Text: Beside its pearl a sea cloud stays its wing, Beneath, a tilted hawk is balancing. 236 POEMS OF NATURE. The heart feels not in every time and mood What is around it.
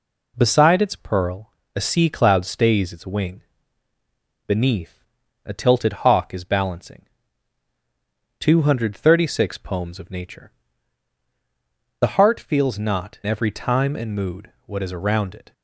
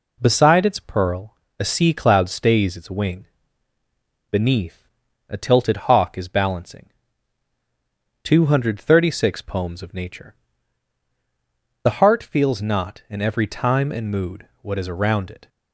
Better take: second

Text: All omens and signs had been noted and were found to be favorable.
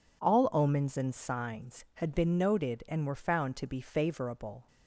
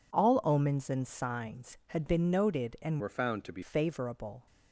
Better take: first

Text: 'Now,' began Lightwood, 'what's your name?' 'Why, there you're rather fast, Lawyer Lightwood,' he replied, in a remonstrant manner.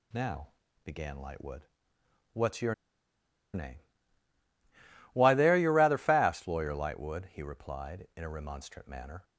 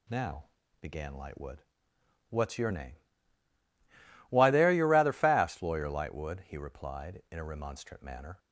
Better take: second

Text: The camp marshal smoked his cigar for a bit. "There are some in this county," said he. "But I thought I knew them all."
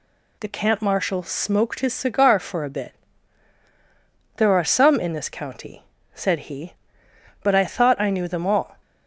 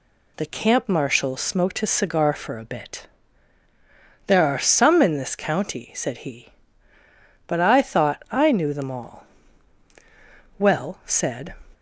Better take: first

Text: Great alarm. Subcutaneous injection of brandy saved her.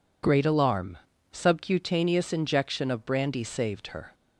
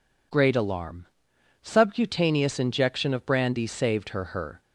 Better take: first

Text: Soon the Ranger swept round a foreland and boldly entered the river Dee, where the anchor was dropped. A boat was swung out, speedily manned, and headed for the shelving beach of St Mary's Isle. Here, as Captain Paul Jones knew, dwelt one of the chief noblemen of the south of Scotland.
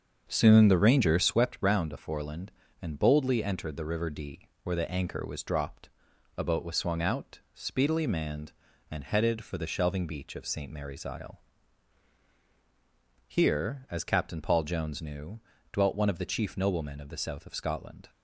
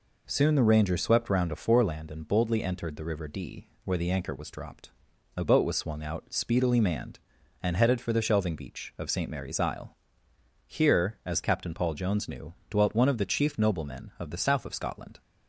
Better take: second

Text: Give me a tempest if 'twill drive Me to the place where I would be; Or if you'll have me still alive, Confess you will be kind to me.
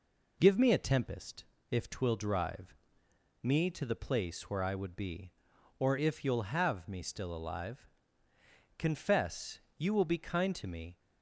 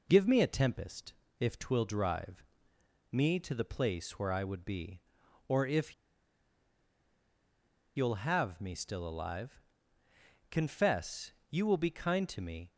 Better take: first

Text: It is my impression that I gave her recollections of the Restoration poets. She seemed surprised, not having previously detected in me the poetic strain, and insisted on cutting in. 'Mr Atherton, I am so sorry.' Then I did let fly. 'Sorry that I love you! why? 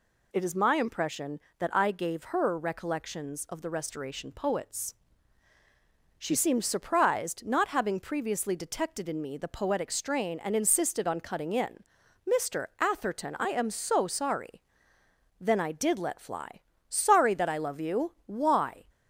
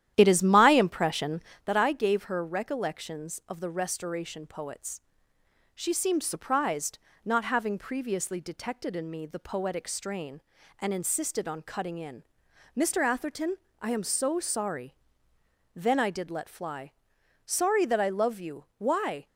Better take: first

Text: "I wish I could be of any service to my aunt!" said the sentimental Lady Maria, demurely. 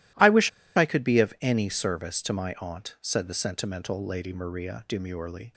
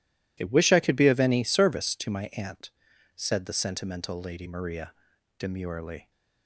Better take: second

